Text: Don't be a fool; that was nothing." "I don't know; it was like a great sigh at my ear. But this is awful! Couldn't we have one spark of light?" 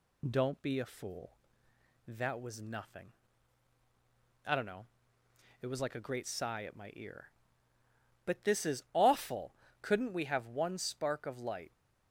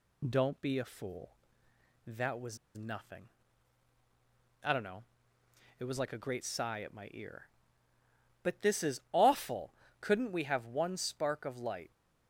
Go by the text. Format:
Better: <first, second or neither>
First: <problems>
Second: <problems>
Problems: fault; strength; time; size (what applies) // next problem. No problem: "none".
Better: first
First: none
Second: pauses between "was" and "nothing"; slight; at 2.5 s; 0.17 s long